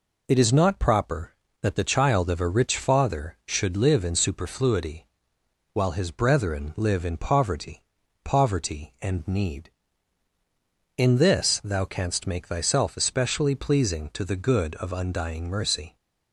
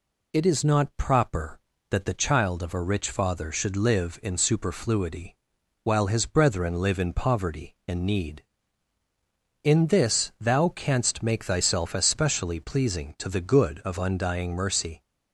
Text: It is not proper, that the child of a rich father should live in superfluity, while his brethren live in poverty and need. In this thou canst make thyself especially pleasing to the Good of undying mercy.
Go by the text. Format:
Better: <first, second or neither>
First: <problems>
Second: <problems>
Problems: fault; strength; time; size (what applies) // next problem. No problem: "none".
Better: second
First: says "poverty" twice; at 8.2 s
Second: none